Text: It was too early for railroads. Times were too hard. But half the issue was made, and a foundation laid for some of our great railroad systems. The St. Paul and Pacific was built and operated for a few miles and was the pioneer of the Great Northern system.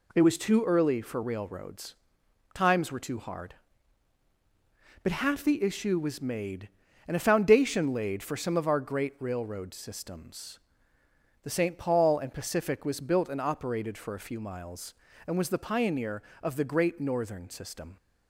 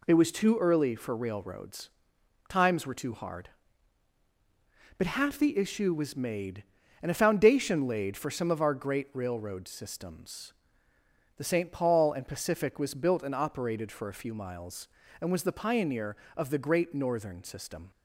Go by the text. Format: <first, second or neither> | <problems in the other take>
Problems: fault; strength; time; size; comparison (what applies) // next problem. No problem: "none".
neither | none